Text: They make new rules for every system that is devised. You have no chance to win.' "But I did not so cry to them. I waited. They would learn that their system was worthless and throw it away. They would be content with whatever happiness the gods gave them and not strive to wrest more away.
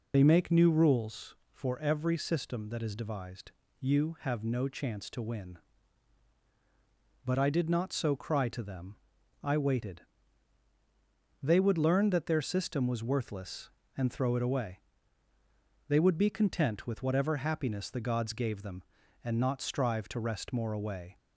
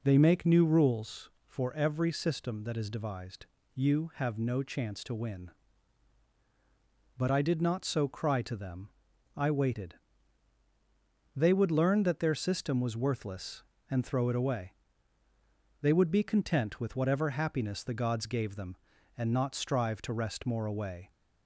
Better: second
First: loses the start of "They"; at 0.1 s; 65 ms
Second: none

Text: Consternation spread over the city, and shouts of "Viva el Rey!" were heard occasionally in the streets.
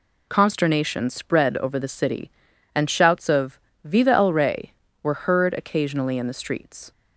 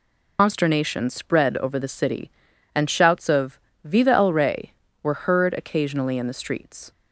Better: first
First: pauses between "of" and "Viva"; slight; at 3.5 s; 0.24 s long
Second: loses the start of "Consternation"; at 0.3 s; 105 ms // pauses between "of" and "Viva"; slight; at 3.5 s; 0.24 s long

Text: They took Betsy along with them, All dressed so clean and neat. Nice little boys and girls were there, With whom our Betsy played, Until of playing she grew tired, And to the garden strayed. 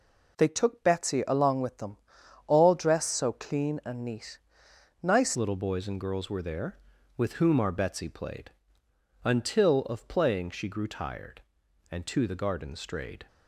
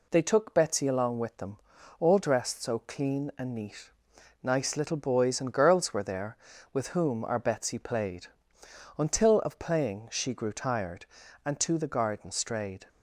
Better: second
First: changes voice at "little"; from 5.3 s on; 7.9 s long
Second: none

